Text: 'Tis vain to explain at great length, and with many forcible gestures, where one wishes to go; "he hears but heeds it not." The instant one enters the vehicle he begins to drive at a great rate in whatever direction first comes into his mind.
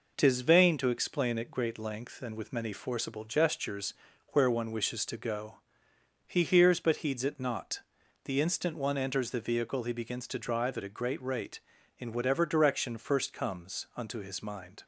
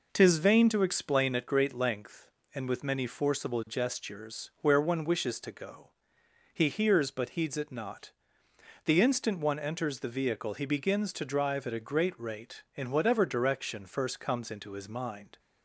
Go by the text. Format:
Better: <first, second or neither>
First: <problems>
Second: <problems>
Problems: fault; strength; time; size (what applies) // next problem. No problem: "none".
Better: second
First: says "unto" for "into"; at 13.9 s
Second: none